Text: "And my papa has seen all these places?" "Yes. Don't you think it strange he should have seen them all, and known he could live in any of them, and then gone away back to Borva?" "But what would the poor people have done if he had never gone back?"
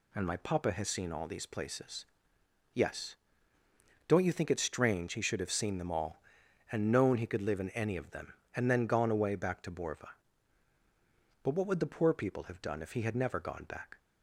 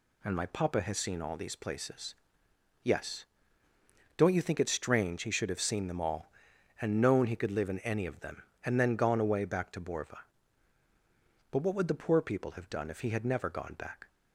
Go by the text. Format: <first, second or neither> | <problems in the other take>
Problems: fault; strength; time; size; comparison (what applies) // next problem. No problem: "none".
neither | none